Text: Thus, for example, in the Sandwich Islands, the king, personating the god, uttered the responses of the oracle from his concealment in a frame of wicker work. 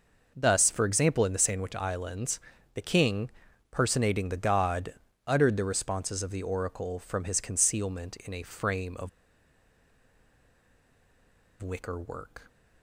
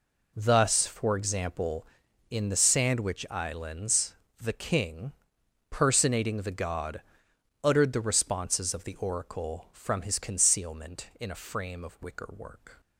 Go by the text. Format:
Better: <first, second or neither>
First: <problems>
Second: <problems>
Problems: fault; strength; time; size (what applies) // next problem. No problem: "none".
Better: second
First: pauses between "of" and "wicker"; strong; at 9.0 s; 2.5 s long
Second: none